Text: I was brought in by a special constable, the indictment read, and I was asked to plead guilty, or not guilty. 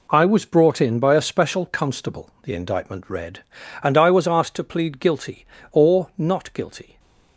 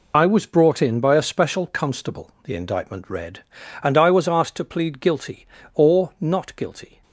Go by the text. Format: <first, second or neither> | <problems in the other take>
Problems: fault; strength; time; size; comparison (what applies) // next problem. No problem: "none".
first | loses the start of "I"; at 0.1 s; 40 ms